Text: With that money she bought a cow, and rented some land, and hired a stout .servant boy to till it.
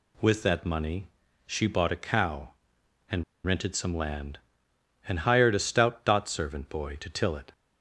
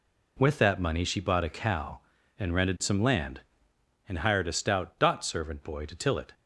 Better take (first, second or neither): second